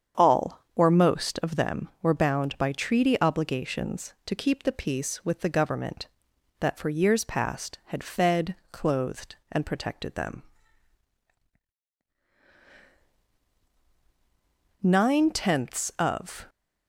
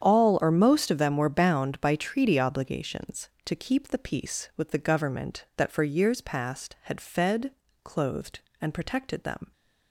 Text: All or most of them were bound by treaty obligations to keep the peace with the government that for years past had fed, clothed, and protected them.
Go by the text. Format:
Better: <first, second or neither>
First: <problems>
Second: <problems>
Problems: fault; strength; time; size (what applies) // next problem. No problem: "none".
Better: second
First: starts louder than the rest; strong; until 1.3 s; 8 dB // goes on to say "Nine tenths of"; from 14.8 s on; 1.6 s long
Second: starts louder than the rest; strong; until 1.0 s; 8.5 dB